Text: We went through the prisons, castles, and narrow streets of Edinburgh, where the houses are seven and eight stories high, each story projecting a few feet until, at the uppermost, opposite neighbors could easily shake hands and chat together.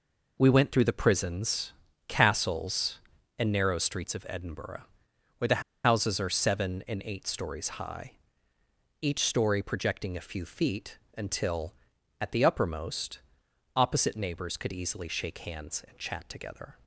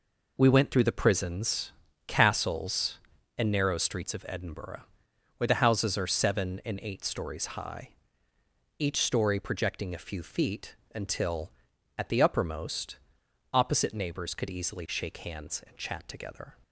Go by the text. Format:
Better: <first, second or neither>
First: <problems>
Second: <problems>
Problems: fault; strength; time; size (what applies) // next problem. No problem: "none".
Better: second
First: pauses between "the" and "houses"; slight; at 5.6 s; 0.24 s long // pauses between "feet" and "until"; slight; at 10.9 s; 0.18 s long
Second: pauses between "feet" and "until"; slight; at 10.7 s; 0.18 s long